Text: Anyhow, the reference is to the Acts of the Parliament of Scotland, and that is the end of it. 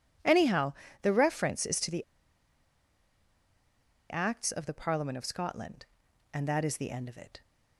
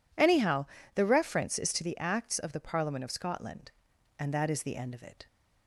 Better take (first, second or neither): second